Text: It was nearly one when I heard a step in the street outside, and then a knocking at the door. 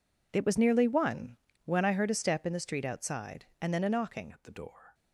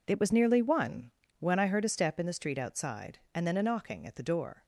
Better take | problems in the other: second | pauses between "one" and "when"; slight; at 1.3 s; 0.28 s long; slight in the second // changes voice at "at"; from 4.3 s on; 0.6 s long

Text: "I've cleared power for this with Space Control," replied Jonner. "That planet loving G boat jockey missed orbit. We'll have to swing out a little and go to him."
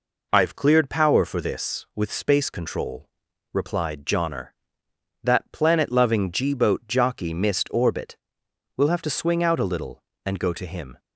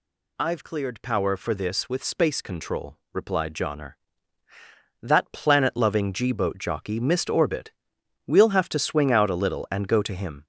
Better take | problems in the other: neither | none

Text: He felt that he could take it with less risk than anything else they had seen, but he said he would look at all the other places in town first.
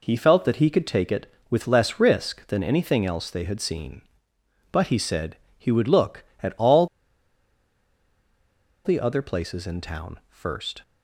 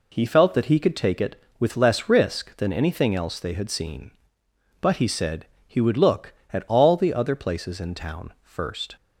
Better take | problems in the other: second | pauses between "said" and "he"; slight; at 5.3 s; 0.20 s long; slight in the second // pauses between "all" and "the"; strong; at 6.8 s; 1.9 s long

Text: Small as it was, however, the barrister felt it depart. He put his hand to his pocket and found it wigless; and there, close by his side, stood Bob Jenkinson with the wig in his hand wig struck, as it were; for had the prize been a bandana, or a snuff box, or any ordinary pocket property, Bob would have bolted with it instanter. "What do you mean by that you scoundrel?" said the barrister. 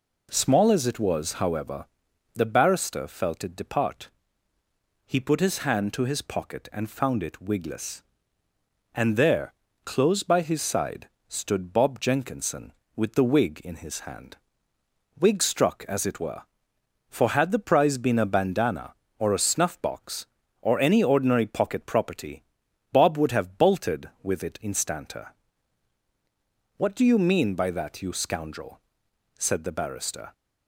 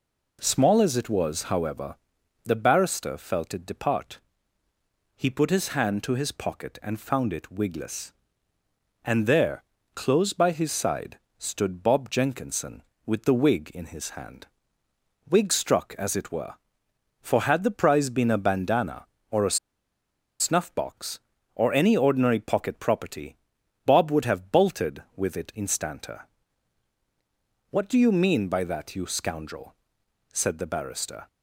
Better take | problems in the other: first | pauses between "hand" and "wig"; noticeable; at 14.4 s; 0.82 s long; noticeable in the first // pauses between "a" and "snuff"; noticeable; at 19.5 s; 0.84 s long

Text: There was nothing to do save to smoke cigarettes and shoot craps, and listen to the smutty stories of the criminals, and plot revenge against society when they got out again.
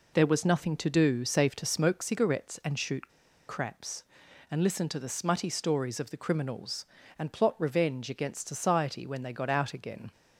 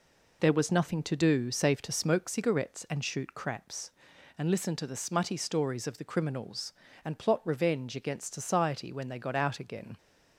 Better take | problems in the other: second | pauses between "shoot" and "craps"; at 3.0 s; 0.40 s long

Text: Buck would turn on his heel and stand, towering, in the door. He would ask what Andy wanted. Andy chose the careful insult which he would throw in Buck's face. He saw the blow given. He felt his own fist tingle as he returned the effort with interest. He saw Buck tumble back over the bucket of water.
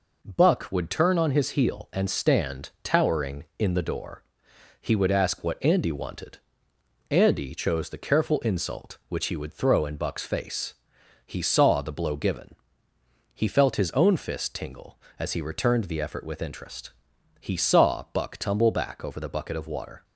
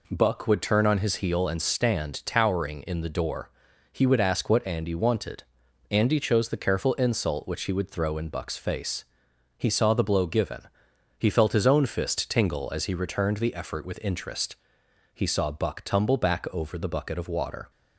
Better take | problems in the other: neither | none

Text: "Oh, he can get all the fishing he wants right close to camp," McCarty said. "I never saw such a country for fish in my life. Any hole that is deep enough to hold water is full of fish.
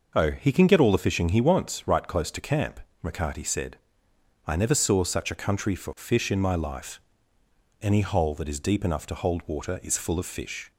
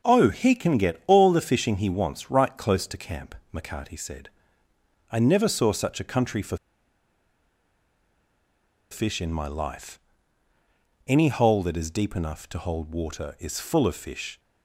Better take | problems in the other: first | pauses between "for" and "fish"; strong; at 6.5 s; 2.3 s long

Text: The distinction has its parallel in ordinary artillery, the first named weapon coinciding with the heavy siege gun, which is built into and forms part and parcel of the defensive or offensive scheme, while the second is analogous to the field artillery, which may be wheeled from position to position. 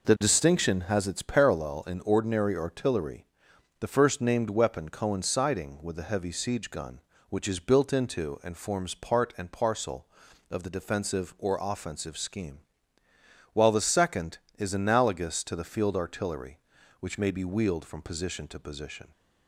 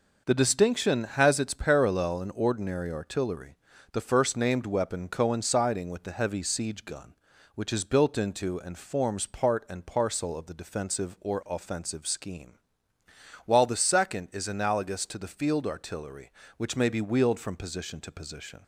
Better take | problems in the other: neither | none

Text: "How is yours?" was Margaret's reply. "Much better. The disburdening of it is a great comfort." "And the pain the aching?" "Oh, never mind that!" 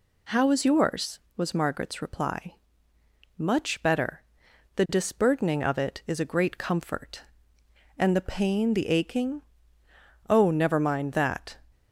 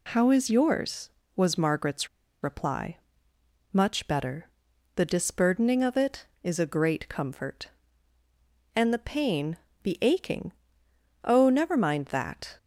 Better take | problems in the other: first | pauses between "Margaret's" and "reply"; slight; at 2.0 s; 0.35 s long // pauses between "pain" and "the"; slight; at 9.5 s; 0.26 s long

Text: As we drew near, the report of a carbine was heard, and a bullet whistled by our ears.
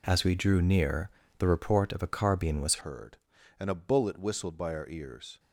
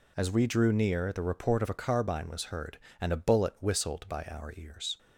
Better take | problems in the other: second | changes voice at "heard"; from 2.8 s on; 2.5 s long

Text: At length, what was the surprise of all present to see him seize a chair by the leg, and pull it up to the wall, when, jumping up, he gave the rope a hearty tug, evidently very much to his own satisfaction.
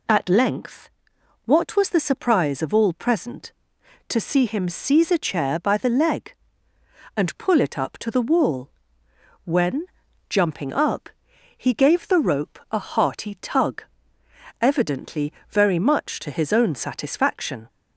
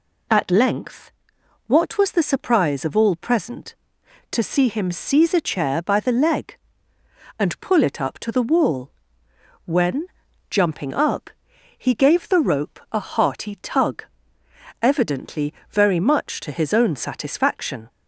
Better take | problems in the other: neither | pauses between "evidently" and "very"; slight; the same in both

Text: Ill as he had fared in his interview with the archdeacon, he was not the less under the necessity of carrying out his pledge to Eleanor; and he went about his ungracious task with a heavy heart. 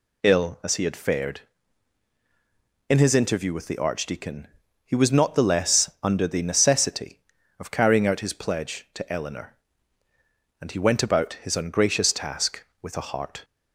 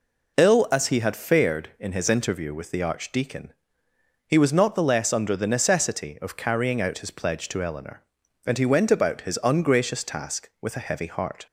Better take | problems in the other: second | skips "heavy"; at 13.0 s

